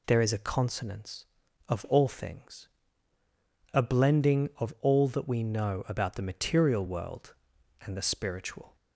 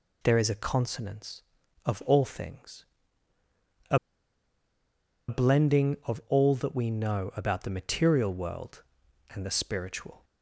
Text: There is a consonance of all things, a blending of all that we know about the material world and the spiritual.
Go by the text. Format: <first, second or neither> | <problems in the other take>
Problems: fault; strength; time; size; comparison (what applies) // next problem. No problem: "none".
first | pauses between "a" and "blending"; strong; at 3.9 s; 1.3 s long